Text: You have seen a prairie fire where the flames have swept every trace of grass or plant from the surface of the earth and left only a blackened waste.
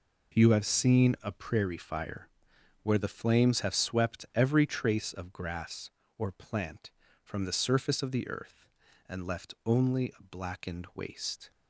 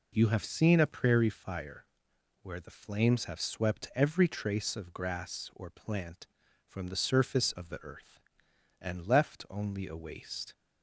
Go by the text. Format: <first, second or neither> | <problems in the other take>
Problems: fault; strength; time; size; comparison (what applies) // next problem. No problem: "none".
first | pauses between "fire" and "where"; noticeable; at 1.8 s; 0.58 s long; noticeable in the first // skips "blackened"; at 9.9 s